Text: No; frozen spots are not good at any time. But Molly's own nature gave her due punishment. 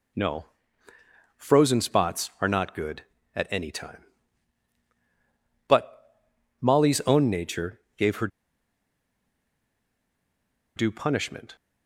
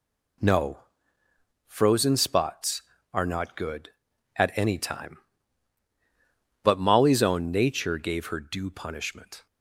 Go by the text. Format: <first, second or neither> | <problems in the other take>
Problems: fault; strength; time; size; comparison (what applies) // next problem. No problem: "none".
second | pauses between "But" and "Molly's"; noticeable; at 6.1 s; 0.48 s long // pauses between "nature" and "gave"; slight; at 7.7 s; 0.18 s long // pauses between "her" and "due"; strong; at 8.2 s; 2.4 s long